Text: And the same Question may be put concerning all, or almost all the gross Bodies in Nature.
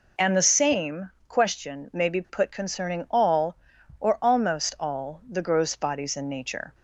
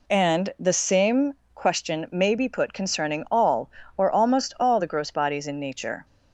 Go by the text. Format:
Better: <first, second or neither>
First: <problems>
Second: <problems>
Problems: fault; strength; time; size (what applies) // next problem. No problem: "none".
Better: neither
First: pauses between "same" and "Question"; slight; at 1.1 s; 0.18 s long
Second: pauses between "same" and "Question"; slight; at 1.3 s; 0.22 s long